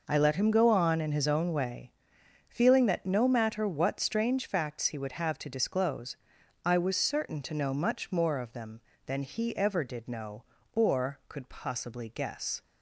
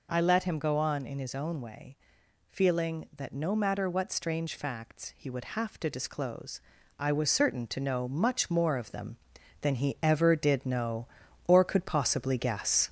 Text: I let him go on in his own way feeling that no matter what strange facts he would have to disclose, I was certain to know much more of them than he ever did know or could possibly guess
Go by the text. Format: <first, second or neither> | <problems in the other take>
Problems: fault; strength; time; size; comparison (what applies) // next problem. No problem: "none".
first | gets louder; slight; throughout; 2.5 dB // pauses between "way" and "feeling"; noticeable; at 1.9 s; 0.54 s long; noticeable in the first